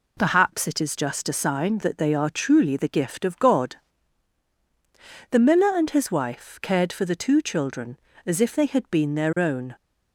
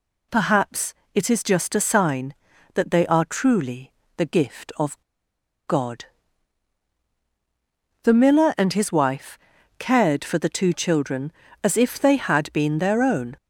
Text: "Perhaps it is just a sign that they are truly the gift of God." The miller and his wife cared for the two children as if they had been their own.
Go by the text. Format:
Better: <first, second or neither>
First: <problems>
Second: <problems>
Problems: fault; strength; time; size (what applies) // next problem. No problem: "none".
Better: first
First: none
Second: pauses between "Perhaps" and "it"; slight; at 0.9 s; 0.22 s long // pauses between "truly" and "the"; slight; at 3.9 s; 0.24 s long // pauses between "of" and "God"; noticeable; at 5.0 s; 0.66 s long // pauses between "wife" and "cared"; at 9.3 s; 0.40 s long